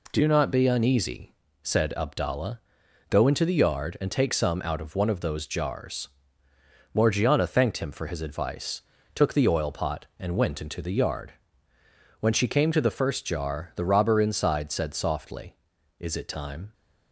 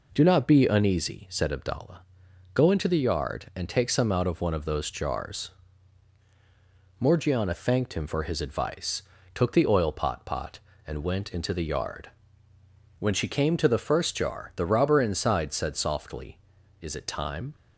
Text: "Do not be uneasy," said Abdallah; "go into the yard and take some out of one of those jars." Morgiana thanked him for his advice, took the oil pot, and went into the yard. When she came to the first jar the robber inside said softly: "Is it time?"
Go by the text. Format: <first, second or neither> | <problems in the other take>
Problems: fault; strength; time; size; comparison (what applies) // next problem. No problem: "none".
first | says "pot" twice; at 10.2 s